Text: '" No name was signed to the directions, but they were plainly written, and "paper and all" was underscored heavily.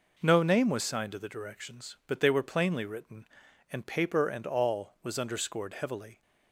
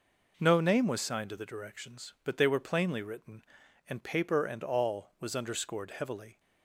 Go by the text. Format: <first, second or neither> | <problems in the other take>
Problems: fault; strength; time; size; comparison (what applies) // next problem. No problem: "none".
neither | none